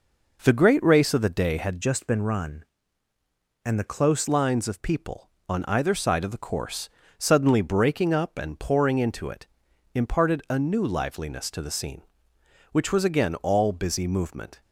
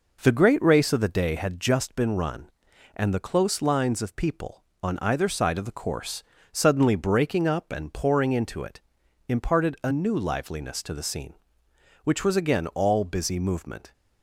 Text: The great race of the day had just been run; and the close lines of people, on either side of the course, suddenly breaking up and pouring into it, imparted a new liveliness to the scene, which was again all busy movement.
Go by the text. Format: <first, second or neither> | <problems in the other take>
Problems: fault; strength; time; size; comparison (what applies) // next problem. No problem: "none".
second | changes voice from "just" to "close"; from 1.8 to 4.2 s; 2.4 s long